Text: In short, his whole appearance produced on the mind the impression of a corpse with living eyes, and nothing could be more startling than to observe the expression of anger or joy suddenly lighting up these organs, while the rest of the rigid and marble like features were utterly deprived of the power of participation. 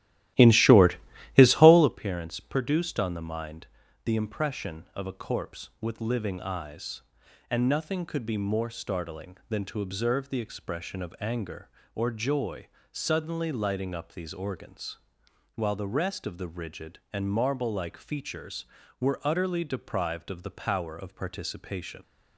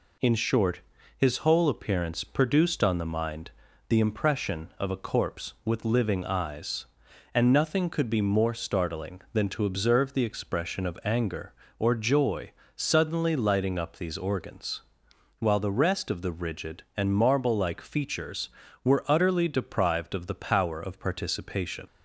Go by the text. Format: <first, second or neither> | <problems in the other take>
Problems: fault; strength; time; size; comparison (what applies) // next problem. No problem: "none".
second | starts louder than the rest; strong; until 2.0 s; 14.5 dB // pauses between "mind" and "the"; slight; at 3.6 s; 0.36 s long; slight in the second // pauses between "joy" and "suddenly"; slight; at 12.6 s; 0.24 s long; slight in the second